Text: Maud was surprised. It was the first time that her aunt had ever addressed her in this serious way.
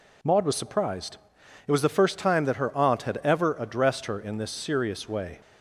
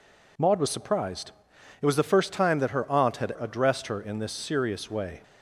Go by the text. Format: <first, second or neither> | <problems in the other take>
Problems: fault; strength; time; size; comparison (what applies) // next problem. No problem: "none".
first | skips "ever"; at 3.3 s